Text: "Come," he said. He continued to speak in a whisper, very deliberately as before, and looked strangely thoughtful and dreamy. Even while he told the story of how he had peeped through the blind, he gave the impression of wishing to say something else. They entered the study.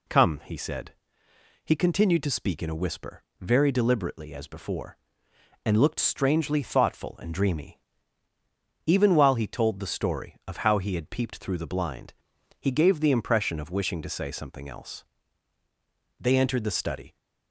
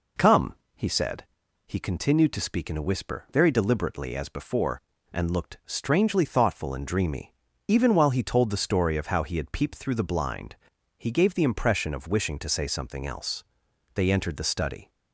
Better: neither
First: none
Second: none

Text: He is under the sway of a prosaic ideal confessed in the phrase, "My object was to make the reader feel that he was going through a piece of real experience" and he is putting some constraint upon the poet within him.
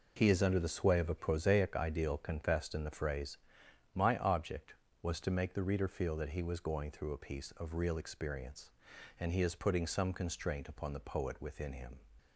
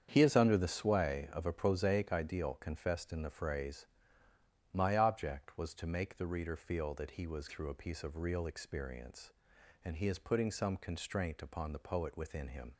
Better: first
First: none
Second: starts louder than the rest; strong; until 1.1 s; 8 dB // skips "going"; at 7.4 s

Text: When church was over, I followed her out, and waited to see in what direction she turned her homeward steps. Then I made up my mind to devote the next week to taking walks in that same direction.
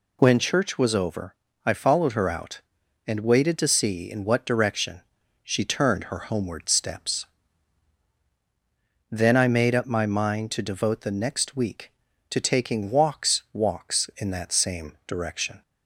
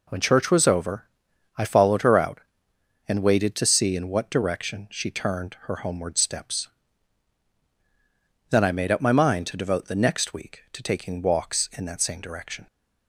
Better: second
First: pauses between "direction" and "she"; at 4.9 s; 0.42 s long // says "walks" twice; at 13.5 s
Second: none

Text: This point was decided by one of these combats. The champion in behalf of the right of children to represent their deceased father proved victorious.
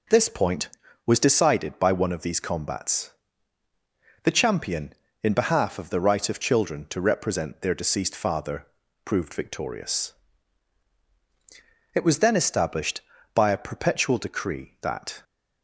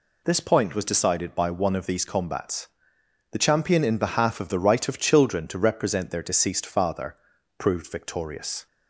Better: second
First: pauses between "father" and "proved"; slight; at 8.6 s; 0.36 s long // goes on to say "It was then established by a perpetual decree that"; strong; from 11.9 s on; 3.2 s long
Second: pauses between "father" and "proved"; at 7.1 s; 0.42 s long

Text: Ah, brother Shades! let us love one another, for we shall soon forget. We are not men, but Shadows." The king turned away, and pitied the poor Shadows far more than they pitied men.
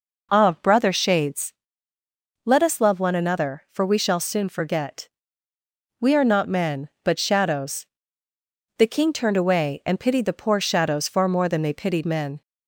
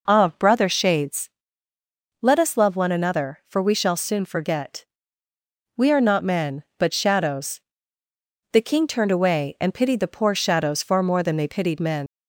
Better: first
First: none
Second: leaves "men" unfinished; at 12.0 s; 95 ms

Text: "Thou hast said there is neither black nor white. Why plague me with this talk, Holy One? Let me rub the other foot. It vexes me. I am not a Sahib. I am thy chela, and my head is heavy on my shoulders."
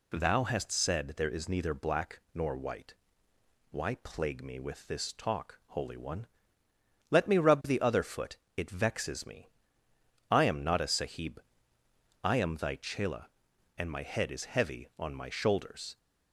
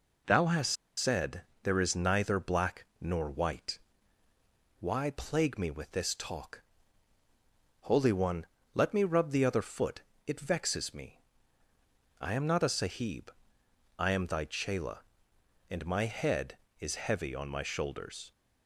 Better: first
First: none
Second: pauses between "hast" and "said"; slight; at 0.7 s; 0.23 s long // pauses between "said" and "there"; slight; at 1.4 s; 0.20 s long // pauses between "black" and "nor"; slight; at 2.8 s; 0.16 s long

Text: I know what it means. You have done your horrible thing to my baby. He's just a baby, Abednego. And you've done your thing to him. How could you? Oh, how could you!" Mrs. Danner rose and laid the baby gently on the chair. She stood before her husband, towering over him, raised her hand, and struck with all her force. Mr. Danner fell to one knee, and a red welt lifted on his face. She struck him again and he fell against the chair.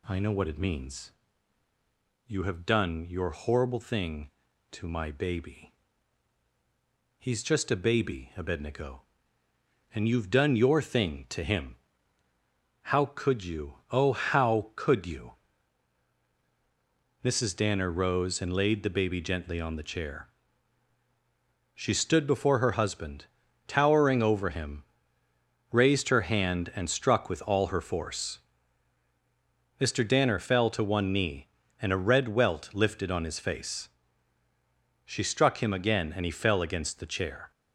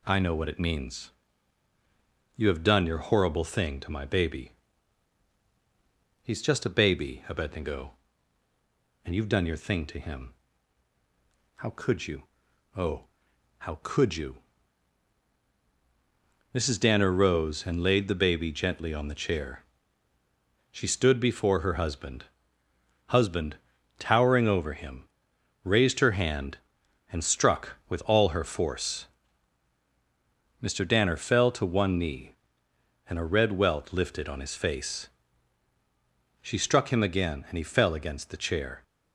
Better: first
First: none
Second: says "husband" twice; at 23.0 s

